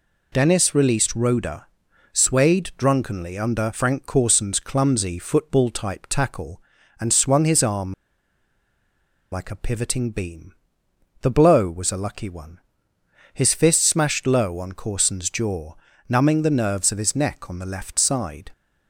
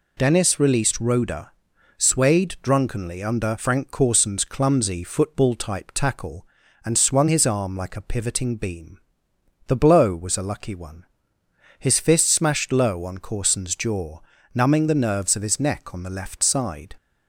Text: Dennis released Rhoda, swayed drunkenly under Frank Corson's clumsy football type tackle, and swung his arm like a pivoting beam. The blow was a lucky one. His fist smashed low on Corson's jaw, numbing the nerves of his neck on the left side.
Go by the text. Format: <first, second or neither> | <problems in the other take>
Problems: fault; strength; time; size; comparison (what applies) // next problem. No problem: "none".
second | pauses between "arm" and "like"; strong; at 7.9 s; 1.3 s long